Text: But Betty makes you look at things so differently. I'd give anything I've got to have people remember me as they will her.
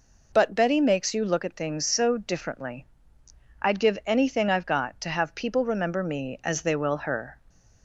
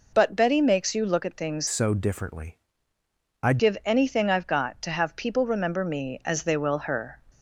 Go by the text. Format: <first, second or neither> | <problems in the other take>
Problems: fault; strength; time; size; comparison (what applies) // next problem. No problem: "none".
first | changes voice from "so" to "I'd"; from 1.6 to 3.5 s; 1.9 s long